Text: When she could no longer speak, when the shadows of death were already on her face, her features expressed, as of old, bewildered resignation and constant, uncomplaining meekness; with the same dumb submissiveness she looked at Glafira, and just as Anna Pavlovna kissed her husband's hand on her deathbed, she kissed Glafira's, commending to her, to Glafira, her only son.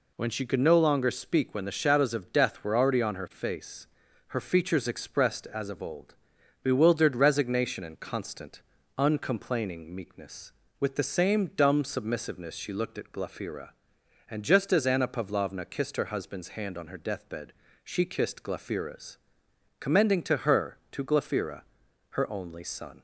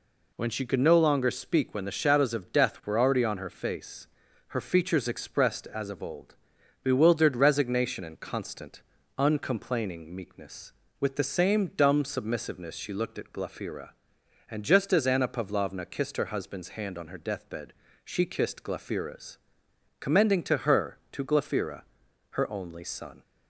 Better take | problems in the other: neither | none

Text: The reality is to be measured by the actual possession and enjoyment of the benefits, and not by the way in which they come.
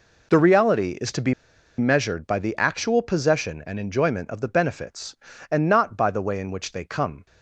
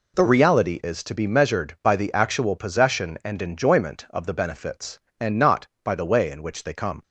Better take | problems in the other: second | pauses between "be" and "measured"; at 1.3 s; 0.45 s long

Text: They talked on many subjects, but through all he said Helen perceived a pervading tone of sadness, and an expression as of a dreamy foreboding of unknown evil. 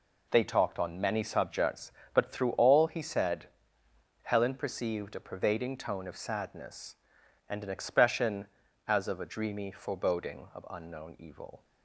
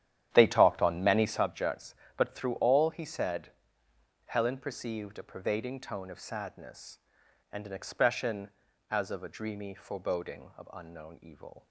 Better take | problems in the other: first | starts louder than the rest; strong; until 1.5 s; 10.5 dB // pauses between "said" and "Helen"; noticeable; at 3.4 s; 0.78 s long; noticeable in the first

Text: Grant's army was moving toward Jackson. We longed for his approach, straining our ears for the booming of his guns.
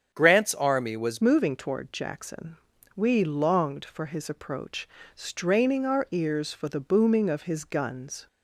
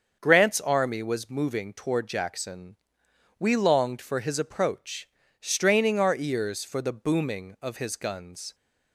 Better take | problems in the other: second | starts louder than the rest; strong; until 1.1 s; 7.5 dB; also in the second // changes voice at "moving"; from 1.2 s on; 7.0 s long

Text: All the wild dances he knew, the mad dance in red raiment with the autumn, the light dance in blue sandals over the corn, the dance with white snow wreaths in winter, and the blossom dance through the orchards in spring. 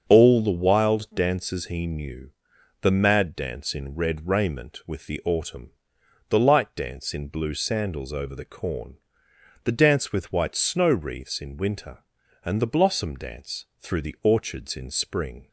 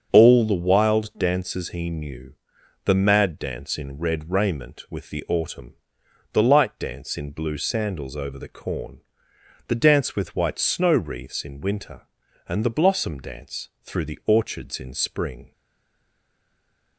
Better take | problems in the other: first | starts louder than the rest; until 1.1 s; 6.5 dB; also in the first // pauses between "dance" and "through"; slight; at 13.6 s; 0.16 s long; slight in the first // stays silent after the last word; noticeable; from 15.5 s on; 1.4 s long

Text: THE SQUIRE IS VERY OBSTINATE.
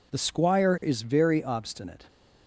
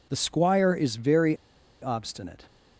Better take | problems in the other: first | pauses between "VERY" and "OBSTINATE"; noticeable; at 1.3 s; 0.46 s long

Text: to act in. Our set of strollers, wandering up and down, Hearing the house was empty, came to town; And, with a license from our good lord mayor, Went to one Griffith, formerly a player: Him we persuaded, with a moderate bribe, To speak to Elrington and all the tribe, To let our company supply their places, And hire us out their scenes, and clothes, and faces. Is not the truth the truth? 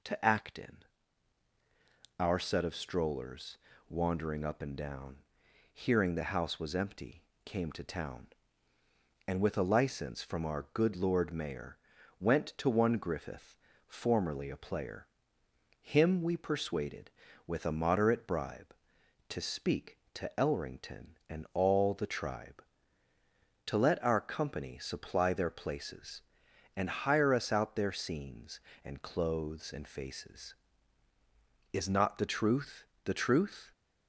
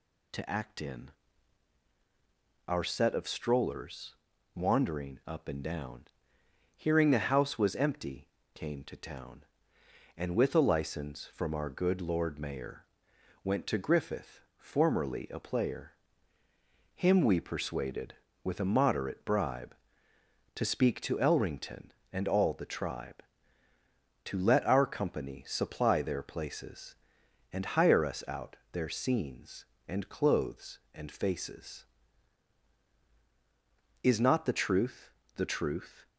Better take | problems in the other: first | skips "one"; at 13.7 s // pauses between "out" and "their"; slight; at 28.5 s; 0.18 s long // pauses between "truth" and "the"; slight; at 35.0 s; 0.26 s long; slight in the first

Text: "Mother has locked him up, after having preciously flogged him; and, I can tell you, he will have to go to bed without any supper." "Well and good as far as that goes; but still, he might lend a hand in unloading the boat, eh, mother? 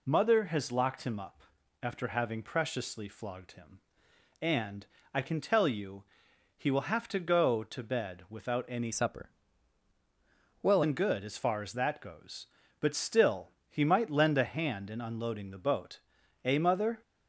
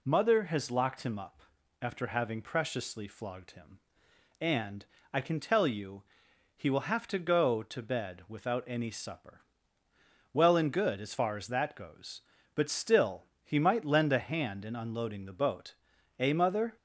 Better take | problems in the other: second | changes voice from "supper" to "Well"; from 8.9 to 10.8 s; 1.9 s long

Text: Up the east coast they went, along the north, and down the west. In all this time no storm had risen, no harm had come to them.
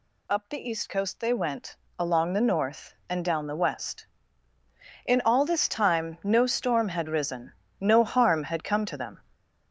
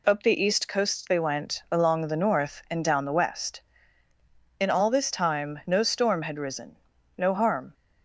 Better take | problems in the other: first | stops before "had come to them"; at 7.7 s

